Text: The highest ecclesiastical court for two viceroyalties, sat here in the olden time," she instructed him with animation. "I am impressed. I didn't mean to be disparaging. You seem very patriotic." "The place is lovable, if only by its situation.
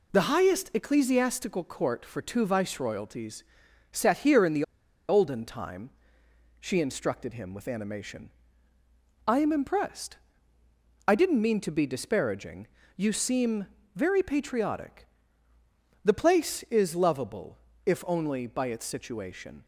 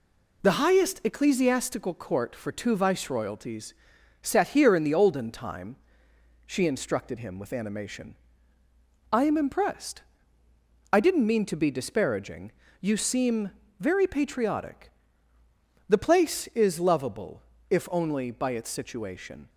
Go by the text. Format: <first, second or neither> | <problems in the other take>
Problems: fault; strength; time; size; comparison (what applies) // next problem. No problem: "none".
second | pauses between "the" and "olden"; at 4.6 s; 0.44 s long // pauses between "seem" and "very"; slight; at 13.6 s; 0.30 s long; slight in the second